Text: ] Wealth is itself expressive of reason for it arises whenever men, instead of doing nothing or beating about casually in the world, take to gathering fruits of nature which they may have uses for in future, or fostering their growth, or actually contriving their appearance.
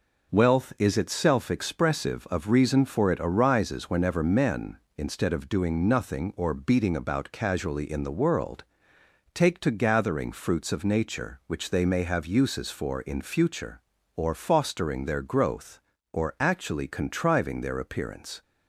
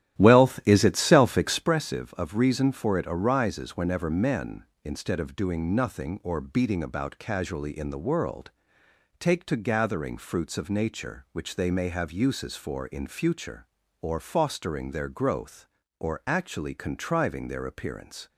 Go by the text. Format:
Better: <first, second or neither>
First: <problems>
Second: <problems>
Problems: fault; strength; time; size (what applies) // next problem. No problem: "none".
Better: first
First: none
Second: starts louder than the rest; strong; until 1.7 s; 12 dB